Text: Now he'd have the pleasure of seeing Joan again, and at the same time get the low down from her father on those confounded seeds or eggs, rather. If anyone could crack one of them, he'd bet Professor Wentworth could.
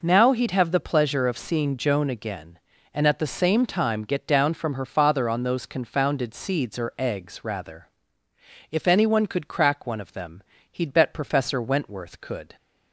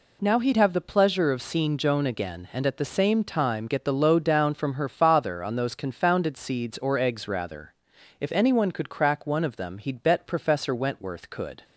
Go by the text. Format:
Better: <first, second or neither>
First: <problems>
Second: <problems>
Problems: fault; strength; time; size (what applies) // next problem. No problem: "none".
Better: second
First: skips "the low"; at 4.2 s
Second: none